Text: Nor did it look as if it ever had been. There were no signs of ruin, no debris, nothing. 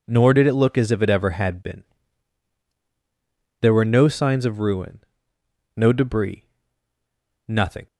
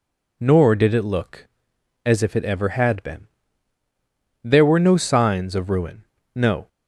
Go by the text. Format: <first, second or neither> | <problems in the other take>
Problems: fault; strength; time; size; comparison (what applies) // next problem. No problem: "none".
first | stops before "debris nothing"; at 6.6 s